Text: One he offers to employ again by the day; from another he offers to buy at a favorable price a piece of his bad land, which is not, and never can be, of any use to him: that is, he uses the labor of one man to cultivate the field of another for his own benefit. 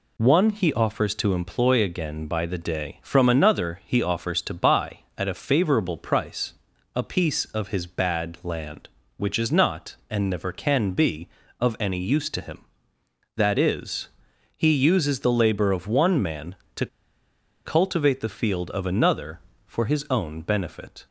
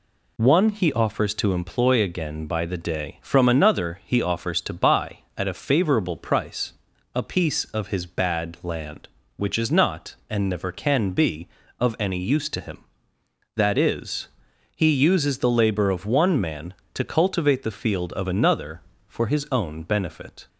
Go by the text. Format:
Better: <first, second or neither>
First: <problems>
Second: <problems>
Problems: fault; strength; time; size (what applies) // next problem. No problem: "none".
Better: second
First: pauses between "price" and "a"; at 6.5 s; 0.40 s long // pauses between "to" and "cultivate"; noticeable; at 16.8 s; 0.78 s long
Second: pauses between "price" and "a"; at 6.7 s; 0.40 s long